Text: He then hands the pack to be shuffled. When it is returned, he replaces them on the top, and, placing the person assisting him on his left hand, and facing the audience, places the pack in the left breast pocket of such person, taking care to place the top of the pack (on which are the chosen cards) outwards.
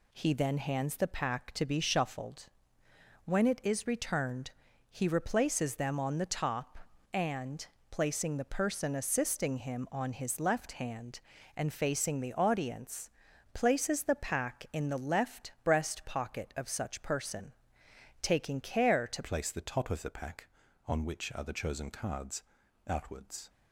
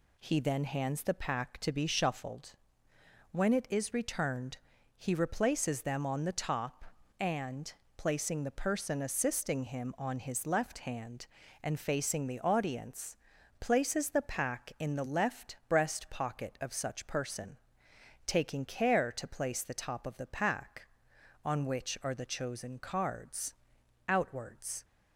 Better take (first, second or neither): second